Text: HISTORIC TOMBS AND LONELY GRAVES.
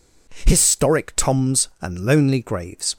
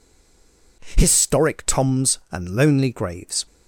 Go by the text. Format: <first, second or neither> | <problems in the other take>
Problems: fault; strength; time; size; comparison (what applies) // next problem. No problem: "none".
first | stays silent before the first word; slight; until 0.8 s; 0.8 s long